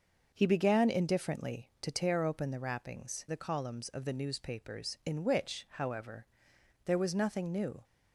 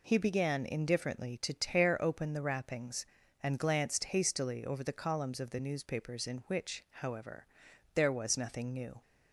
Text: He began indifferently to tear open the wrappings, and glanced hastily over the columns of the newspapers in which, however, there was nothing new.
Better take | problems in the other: second | starts louder than the rest; noticeable; until 1.3 s; 6 dB // skips "and glanced hastily over"; at 3.2 s

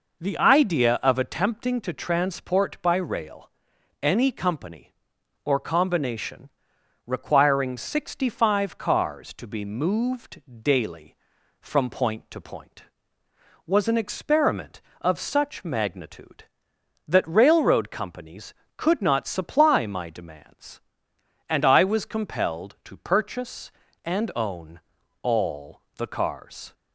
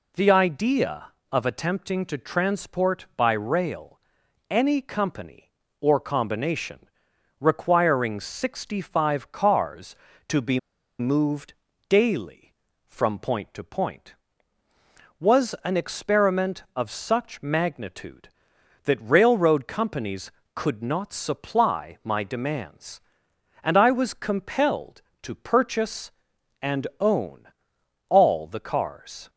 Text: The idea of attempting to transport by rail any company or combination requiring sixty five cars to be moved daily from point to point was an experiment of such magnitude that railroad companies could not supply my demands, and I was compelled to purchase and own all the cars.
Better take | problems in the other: first | pauses between "rail" and "any"; noticeable; at 3.9 s; 0.52 s long; noticeable in the first // pauses between "combination" and "requiring"; noticeable; at 6.7 s; 0.60 s long; noticeable in the first // pauses between "be" and "moved"; at 10.5 s; 0.39 s long // pauses between "moved" and "daily"; slight; at 11.5 s; 0.34 s long; slight in the first // pauses between "own" and "all"; noticeable; at 27.4 s; 0.62 s long; also in the first

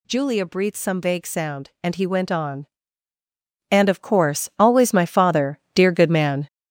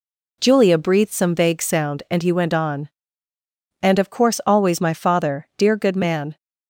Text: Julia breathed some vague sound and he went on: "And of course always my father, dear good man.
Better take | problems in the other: second | gets louder; strong; throughout; 7.5 dB

